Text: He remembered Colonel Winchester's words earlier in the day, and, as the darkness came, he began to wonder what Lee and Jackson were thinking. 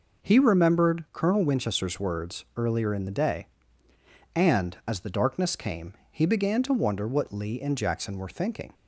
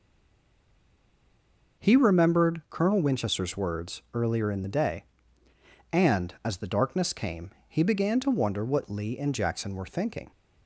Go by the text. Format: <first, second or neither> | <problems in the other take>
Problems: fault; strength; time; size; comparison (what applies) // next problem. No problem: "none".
first | stays silent before the first word; noticeable; until 1.7 s; 1.7 s long